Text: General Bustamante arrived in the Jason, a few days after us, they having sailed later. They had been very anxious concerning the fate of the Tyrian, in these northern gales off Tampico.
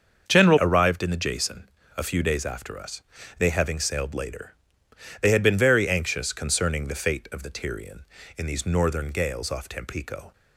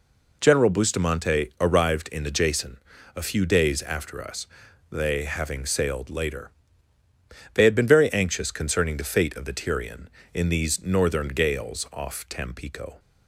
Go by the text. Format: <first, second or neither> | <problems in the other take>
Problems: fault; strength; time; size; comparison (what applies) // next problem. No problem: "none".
second | starts louder than the rest; until 1.2 s; 6.5 dB // skips "Bustamante"; at 0.5 s